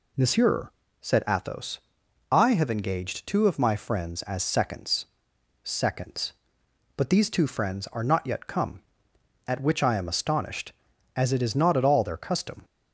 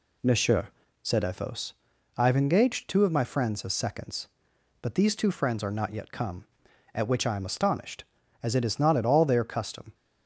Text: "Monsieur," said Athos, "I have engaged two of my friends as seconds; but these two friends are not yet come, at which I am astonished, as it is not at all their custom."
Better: second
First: says "seconds" twice; at 5.6 s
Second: none

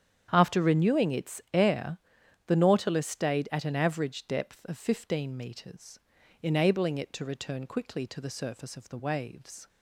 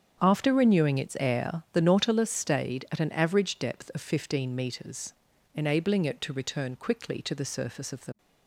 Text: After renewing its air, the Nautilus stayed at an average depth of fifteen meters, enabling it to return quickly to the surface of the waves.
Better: first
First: starts louder than the rest; strong; until 1.3 s; 9 dB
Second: starts louder than the rest; strong; until 1.2 s; 8 dB // stops before "waves"; at 8.1 s

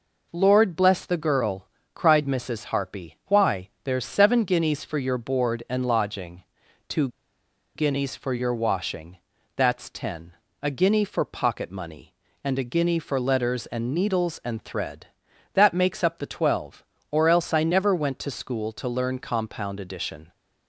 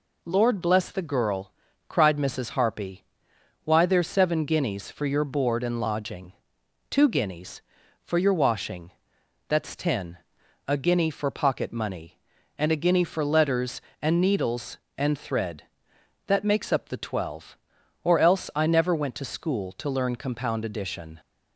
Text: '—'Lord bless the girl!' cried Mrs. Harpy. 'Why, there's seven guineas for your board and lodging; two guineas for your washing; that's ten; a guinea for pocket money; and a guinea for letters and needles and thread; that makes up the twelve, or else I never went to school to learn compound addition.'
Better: second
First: pauses between "two" and "guineas"; noticeable; at 7.0 s; 0.67 s long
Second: none

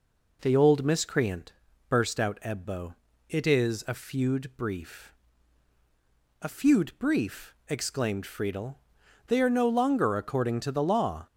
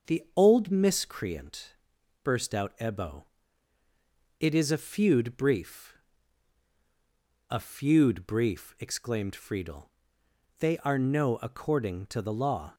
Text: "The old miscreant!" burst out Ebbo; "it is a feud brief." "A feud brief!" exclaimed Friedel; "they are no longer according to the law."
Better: first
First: none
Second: starts louder than the rest; noticeable; until 1.1 s; 6 dB // skips "longer"; at 11.3 s

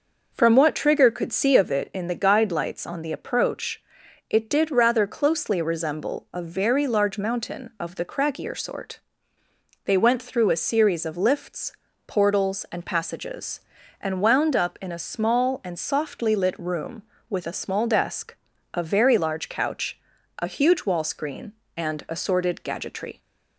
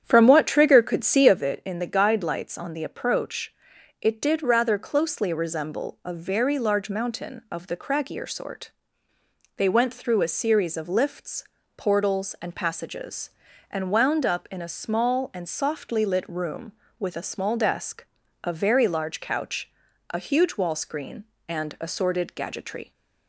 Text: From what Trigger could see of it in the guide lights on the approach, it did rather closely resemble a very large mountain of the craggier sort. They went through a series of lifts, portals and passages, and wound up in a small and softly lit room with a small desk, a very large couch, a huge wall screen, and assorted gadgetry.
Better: first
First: none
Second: starts louder than the rest; strong; until 1.4 s; 9 dB

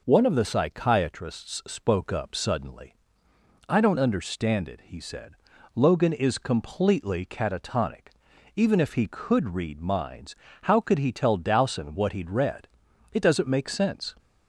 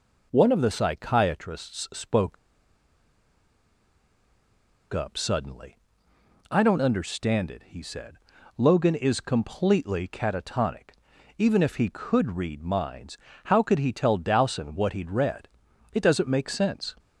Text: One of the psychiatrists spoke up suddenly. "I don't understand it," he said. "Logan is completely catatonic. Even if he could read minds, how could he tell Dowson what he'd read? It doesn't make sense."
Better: first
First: none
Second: pauses between "spoke" and "up"; strong; at 2.3 s; 2.5 s long

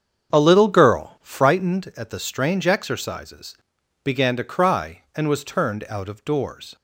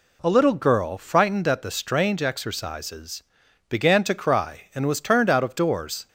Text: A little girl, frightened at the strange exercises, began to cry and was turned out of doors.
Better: second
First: starts louder than the rest; strong; until 1.5 s; 7.5 dB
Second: none

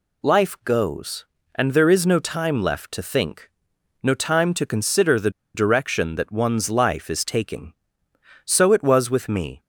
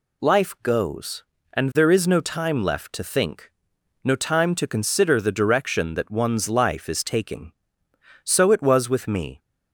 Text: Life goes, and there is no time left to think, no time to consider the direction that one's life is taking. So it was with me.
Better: second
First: pauses between "the" and "direction"; slight; at 5.2 s; 0.24 s long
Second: none

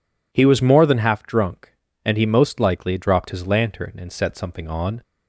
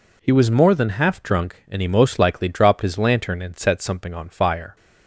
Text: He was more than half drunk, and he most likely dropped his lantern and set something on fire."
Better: second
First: stops before "fire"; at 5.0 s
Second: none

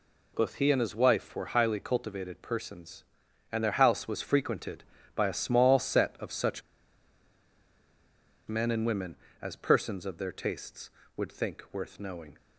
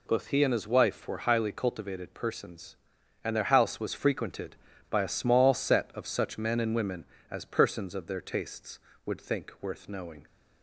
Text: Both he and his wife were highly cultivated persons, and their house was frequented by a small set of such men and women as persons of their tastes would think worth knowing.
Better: second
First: pauses between "such" and "men"; strong; at 6.6 s; 1.8 s long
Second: none

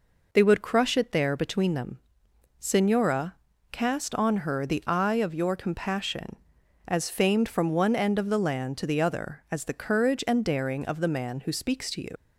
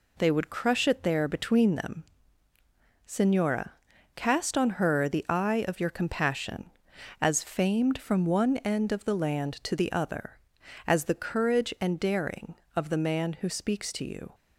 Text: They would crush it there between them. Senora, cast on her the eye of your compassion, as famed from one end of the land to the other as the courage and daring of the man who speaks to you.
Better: second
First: leaves "you" unfinished; at 12.1 s; 90 ms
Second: none

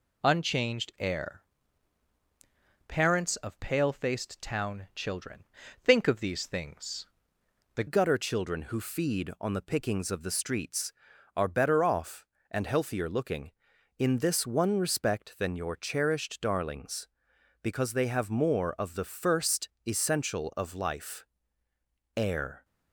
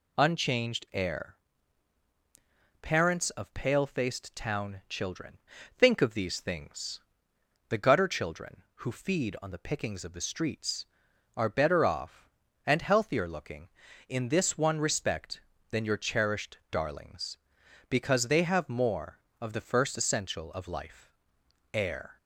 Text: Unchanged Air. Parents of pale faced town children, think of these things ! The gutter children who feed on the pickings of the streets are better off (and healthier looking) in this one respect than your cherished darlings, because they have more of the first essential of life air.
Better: second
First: changes voice at "gutter"; from 7.8 s on; 14.8 s long // pauses between "first" and "essential"; slight; at 19.6 s; 0.16 s long // pauses between "life" and "air"; noticeable; at 21.2 s; 0.88 s long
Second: pauses between "life" and "air"; noticeable; at 21.0 s; 0.64 s long

